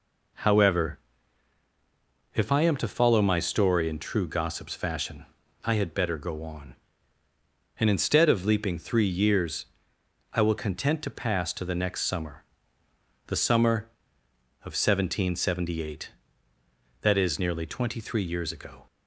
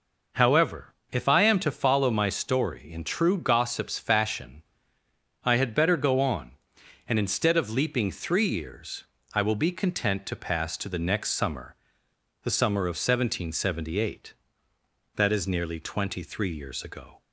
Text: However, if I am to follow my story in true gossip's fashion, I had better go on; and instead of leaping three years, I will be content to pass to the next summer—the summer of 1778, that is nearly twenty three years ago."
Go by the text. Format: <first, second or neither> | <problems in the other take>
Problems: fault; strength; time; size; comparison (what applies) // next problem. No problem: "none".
second | skips "be"; at 10.5 s